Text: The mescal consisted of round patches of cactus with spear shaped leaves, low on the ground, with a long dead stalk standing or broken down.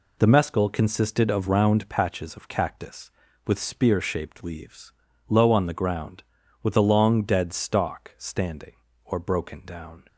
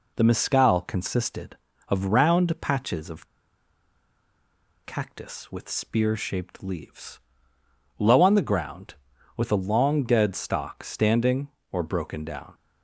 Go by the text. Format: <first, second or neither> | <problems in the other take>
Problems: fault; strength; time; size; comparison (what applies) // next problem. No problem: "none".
first | pauses between "of" and "cactus"; strong; at 3.2 s; 1.5 s long